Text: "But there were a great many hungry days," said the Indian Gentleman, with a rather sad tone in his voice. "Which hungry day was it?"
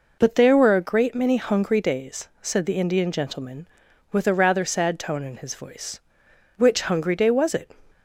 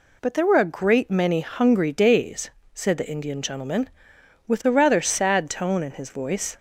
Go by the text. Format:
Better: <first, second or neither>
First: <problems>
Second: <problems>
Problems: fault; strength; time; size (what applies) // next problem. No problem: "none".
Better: first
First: none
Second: stops before "Which hungry day was it"; at 6.5 s